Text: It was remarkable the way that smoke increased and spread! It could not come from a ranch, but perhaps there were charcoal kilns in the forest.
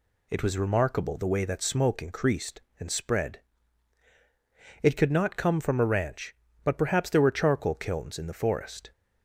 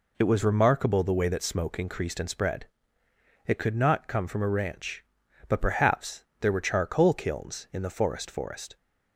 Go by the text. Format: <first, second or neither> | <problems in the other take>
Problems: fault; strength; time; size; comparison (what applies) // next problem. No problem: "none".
first | pauses between "perhaps" and "there"; slight; at 6.2 s; 0.16 s long // says "forest" twice; at 8.3 s